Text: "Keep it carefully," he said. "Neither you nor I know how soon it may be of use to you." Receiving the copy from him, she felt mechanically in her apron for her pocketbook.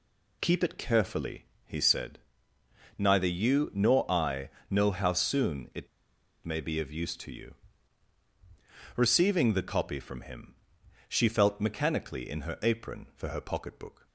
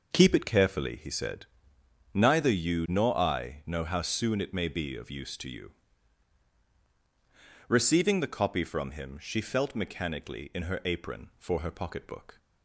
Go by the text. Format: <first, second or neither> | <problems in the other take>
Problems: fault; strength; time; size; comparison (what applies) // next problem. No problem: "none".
second | pauses between "I" and "know"; slight; at 4.4 s; 0.22 s long // pauses between "it" and "may"; noticeable; at 5.8 s; 0.58 s long